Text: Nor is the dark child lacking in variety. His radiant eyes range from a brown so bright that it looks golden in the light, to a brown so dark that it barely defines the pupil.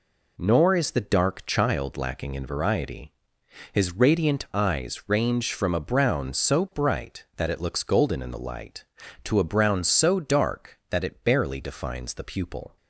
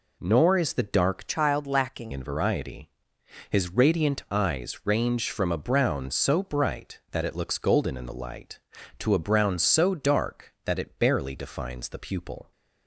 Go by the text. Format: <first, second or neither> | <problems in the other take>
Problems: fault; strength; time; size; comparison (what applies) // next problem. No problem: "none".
first | changes voice from "child" to "lacking"; from 1.2 to 2.1 s; 0.9 s long